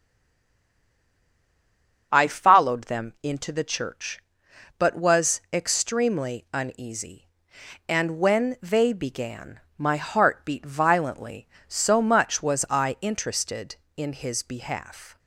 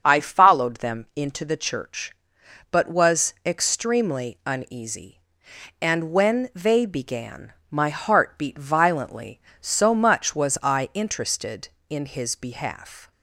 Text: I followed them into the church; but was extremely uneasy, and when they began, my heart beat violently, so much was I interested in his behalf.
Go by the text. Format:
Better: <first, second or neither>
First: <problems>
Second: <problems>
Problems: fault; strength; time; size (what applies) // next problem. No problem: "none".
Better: second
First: stays silent before the first word; until 2.1 s; 2.1 s long // starts louder than the rest; until 3.1 s; 7 dB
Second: starts louder than the rest; until 1.0 s; 7 dB